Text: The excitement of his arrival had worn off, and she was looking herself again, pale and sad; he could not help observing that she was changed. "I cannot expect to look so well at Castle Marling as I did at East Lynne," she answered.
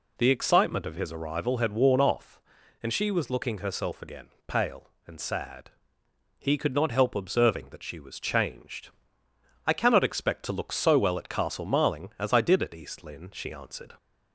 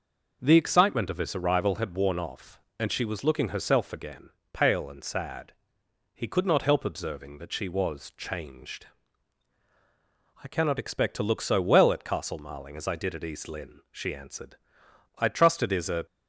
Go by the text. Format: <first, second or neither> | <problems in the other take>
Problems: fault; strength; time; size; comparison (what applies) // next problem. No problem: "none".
first | goes on to say "I trust it is a"; noticeable; from 15.1 s on; 0.88 s long